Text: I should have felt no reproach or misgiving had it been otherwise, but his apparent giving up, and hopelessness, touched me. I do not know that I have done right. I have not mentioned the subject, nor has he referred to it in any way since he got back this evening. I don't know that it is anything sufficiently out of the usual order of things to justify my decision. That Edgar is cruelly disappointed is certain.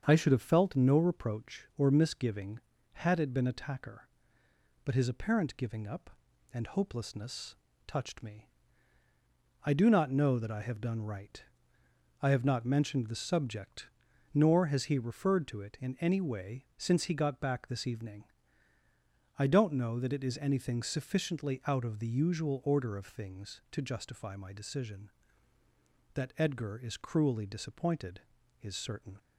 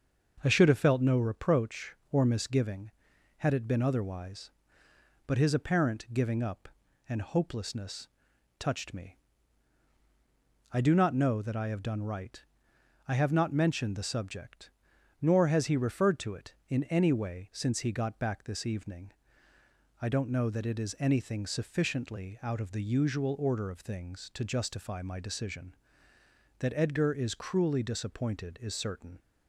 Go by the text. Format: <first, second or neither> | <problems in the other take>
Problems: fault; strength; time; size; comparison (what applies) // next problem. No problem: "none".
second | starts louder than the rest; strong; until 1.0 s; 7 dB; also in the second // says "attacker" for "otherwise"; at 3.4 s